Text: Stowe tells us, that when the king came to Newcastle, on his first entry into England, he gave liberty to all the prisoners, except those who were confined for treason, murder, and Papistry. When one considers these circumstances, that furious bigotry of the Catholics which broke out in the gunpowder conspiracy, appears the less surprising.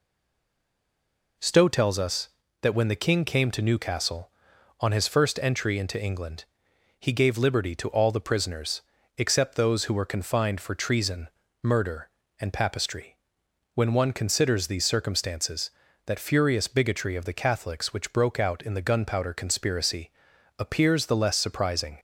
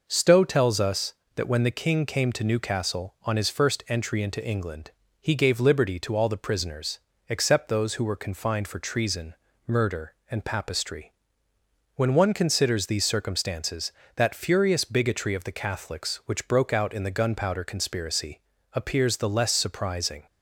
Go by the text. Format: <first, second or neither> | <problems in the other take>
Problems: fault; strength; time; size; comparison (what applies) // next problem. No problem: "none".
second | stays silent before the first word; noticeable; until 1.3 s; 1.3 s long